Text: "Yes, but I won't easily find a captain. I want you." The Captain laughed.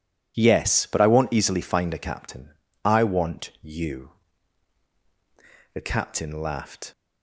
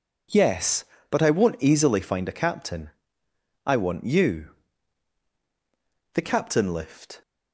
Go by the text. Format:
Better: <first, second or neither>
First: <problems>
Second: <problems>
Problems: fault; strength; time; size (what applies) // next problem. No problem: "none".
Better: first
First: none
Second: says "lift" for "laughed"; at 6.7 s